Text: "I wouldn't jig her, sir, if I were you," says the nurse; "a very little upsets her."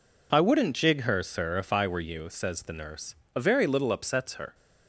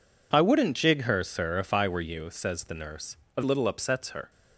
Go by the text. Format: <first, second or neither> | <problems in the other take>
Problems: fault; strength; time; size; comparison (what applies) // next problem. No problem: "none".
first | skips "very"; at 3.4 s